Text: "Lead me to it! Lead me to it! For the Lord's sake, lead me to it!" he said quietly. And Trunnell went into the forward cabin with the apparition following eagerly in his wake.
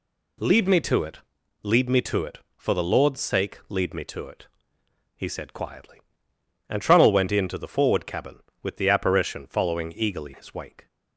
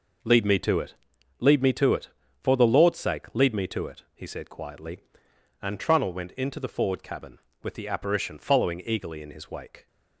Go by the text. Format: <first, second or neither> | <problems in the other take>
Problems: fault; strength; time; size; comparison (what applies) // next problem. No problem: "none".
second | skips "in"; at 10.3 s